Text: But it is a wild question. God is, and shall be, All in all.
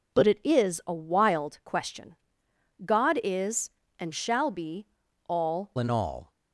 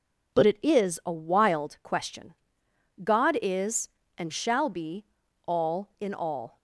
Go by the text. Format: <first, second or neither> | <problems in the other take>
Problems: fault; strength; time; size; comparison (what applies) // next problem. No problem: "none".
second | changes voice at "in"; from 5.7 s on; 0.6 s long